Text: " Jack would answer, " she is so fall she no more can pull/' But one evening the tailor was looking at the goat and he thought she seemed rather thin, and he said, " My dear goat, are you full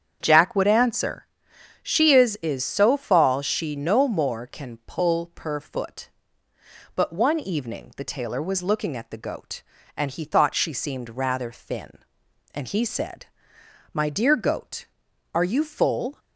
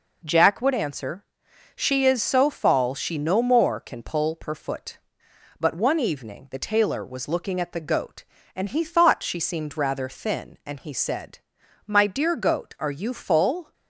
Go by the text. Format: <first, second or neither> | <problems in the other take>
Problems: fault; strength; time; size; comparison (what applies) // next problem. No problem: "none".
second | starts louder than the rest; strong; until 1.2 s; 8 dB // says "is" twice; at 2.4 s